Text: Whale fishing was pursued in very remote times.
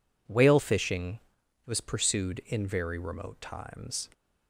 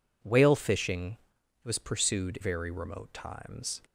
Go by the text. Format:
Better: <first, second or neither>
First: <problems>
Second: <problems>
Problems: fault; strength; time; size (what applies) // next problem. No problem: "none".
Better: first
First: none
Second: skips "in"; at 2.3 s